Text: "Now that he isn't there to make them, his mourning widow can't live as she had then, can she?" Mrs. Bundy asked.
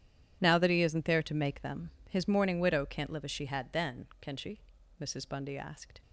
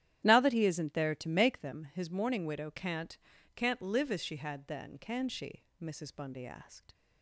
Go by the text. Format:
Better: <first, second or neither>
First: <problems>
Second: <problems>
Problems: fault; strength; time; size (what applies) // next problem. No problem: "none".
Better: first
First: none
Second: starts louder than the rest; strong; until 1.2 s; 12.5 dB // says "can't" twice; at 3.5 s